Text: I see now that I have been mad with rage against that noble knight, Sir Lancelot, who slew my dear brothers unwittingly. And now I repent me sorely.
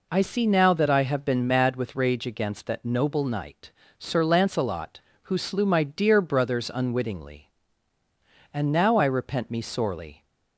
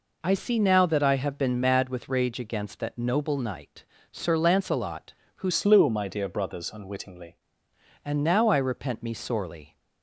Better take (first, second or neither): first